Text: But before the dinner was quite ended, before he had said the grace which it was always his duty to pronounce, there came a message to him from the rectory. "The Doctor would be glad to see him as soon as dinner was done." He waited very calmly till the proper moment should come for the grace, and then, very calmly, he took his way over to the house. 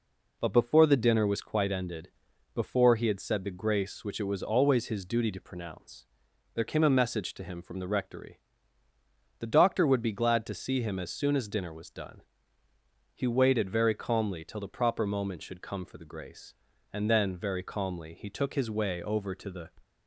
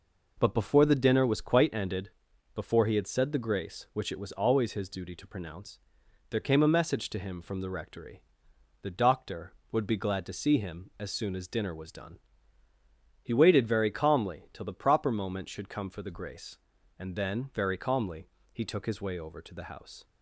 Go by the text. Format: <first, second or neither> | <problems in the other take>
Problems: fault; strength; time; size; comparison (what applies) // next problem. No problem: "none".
second | stops before "house"; at 19.8 s